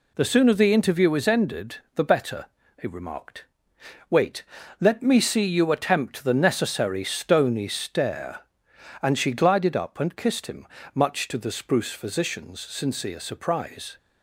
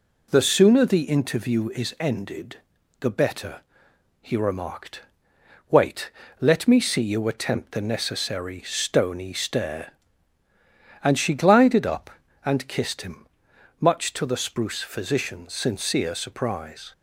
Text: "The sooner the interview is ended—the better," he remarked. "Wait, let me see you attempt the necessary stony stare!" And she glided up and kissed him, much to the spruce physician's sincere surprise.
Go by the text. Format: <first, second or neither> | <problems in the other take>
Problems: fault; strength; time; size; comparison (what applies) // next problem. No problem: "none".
neither | none